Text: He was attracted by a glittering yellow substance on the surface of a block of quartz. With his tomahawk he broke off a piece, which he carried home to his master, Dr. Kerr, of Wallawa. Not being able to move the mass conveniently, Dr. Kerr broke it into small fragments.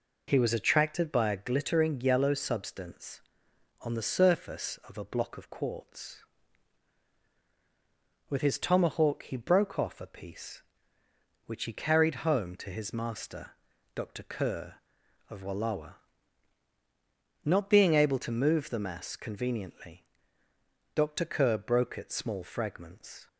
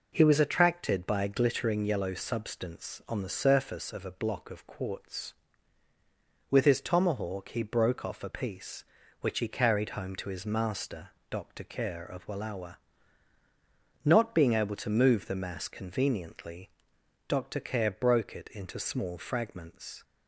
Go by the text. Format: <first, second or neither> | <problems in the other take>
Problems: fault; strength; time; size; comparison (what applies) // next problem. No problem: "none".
second | skips "into"; at 22.1 s